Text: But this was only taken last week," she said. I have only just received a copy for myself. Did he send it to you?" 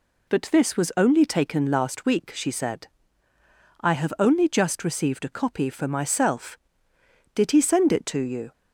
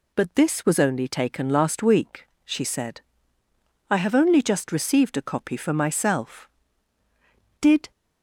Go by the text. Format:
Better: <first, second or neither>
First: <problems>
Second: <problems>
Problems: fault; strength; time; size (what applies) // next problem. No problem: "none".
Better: first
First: none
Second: stops before "he send it to you"; at 7.9 s